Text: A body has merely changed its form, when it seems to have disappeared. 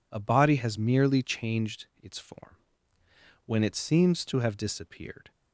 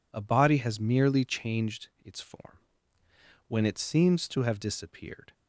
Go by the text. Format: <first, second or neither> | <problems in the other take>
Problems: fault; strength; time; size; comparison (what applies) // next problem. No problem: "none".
neither | none